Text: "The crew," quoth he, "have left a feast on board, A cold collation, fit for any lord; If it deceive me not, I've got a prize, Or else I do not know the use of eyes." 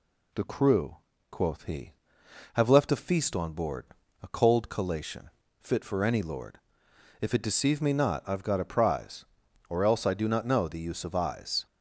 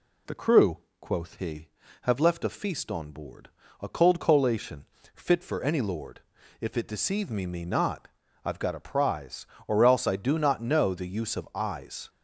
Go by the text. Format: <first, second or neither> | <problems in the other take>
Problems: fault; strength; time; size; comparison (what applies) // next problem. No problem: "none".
first | says "me" twice; at 7.4 s